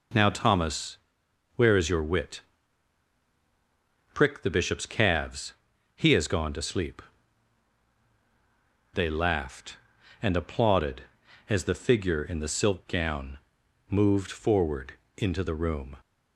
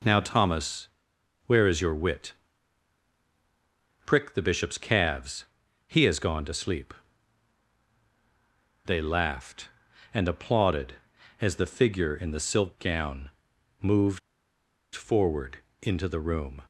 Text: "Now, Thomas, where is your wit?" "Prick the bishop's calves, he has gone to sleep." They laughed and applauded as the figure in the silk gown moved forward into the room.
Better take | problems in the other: first | pauses between "gown" and "moved"; noticeable; at 13.3 s; 0.50 s long; noticeable in the first // pauses between "moved" and "forward"; noticeable; at 14.1 s; 0.75 s long // pauses between "forward" and "into"; slight; at 15.6 s; 0.18 s long; slight in the first

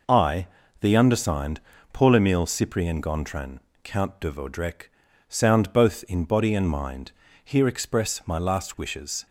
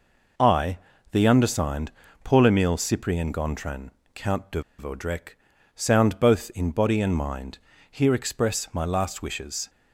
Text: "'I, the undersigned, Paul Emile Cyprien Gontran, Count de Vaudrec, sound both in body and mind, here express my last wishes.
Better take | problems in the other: first | pauses between "de" and "Vaudrec"; slight; at 4.6 s; 0.16 s long

